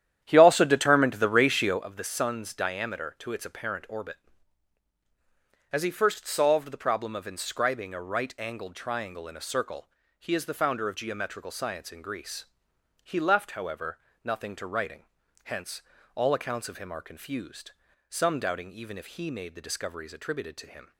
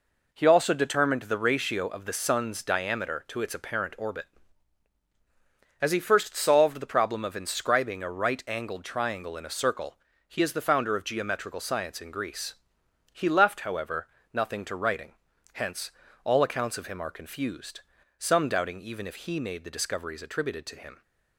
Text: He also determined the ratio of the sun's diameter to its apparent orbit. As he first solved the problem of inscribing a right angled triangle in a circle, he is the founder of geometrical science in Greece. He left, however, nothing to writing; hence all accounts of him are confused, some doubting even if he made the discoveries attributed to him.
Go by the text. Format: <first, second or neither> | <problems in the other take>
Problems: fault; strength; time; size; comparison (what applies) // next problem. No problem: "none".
second | starts louder than the rest; strong; until 1.9 s; 10.5 dB // pauses between "hence" and "all"; slight; at 15.8 s; 0.34 s long; slight in the second